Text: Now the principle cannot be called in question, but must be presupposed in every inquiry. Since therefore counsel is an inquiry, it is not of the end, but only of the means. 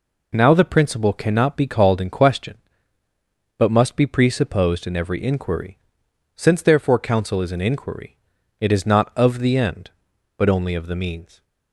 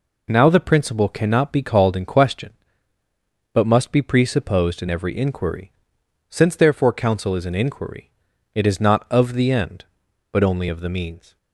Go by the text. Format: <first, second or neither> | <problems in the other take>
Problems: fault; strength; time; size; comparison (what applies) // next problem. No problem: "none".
neither | none